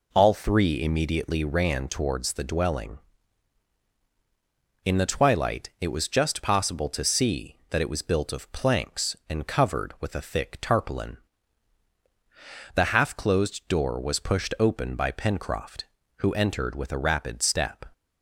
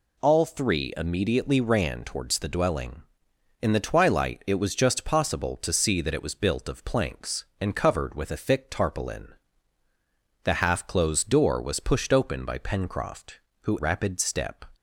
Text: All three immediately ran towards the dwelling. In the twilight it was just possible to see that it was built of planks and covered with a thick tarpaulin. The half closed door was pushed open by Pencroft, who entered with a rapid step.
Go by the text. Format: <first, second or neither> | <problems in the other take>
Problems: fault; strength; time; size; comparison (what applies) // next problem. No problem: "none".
first | skips "entered with a"; at 13.7 s